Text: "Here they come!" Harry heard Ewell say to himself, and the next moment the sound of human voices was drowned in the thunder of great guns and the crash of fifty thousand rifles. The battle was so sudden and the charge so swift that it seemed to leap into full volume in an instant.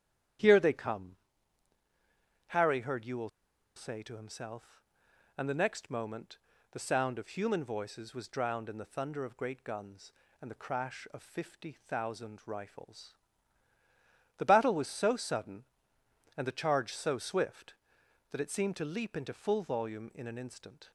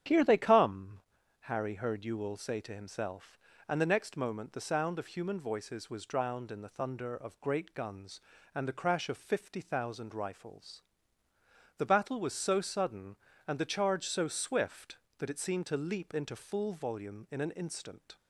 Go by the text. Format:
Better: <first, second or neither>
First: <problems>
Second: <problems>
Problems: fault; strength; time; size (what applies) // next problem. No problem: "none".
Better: second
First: starts louder than the rest; strong; until 2.7 s; 10 dB // pauses between "Ewell" and "say"; noticeable; at 3.2 s; 0.47 s long // pauses between "moment" and "the"; slight; at 6.3 s; 0.32 s long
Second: starts louder than the rest; strong; until 1.4 s; 9 dB